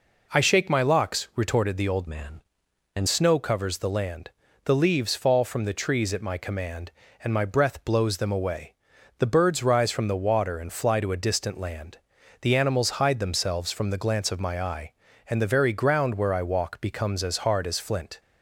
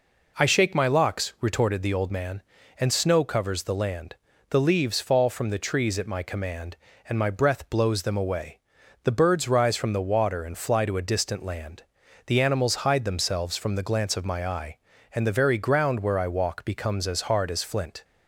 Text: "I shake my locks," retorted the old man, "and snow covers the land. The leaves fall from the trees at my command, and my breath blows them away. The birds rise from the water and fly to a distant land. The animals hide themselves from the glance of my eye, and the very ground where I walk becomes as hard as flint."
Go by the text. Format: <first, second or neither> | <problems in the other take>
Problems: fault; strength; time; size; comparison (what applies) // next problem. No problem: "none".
second | changes voice from "man" to "and"; from 2.0 to 3.0 s; 1.0 s long